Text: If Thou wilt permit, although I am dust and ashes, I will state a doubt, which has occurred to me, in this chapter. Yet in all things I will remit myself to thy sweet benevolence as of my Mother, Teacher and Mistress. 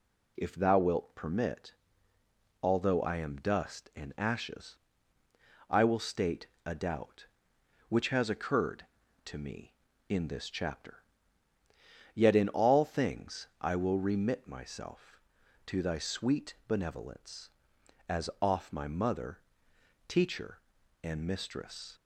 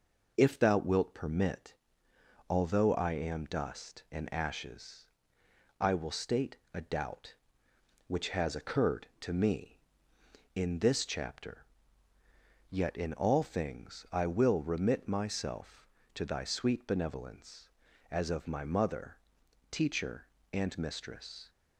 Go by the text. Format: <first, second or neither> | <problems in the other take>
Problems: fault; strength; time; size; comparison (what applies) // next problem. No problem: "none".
second | pauses between "state" and "a"; slight; at 6.4 s; 0.20 s long; slight in the second // says "off" for "of"; at 18.4 s